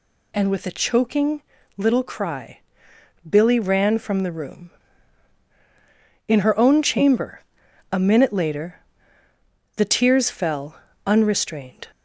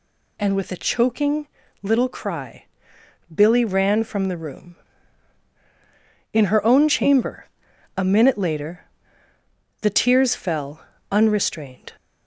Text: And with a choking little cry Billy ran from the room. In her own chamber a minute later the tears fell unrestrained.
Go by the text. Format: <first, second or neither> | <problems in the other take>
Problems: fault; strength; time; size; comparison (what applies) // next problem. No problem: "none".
neither | pauses between "choking" and "little"; slight; the same in both // pauses between "cry" and "Billy"; noticeable; the same in both // pauses between "chamber" and "a"; noticeable; the same in both // pauses between "later" and "the"; noticeable; the same in both // pauses between "fell" and "unrestrained"; slight; the same in both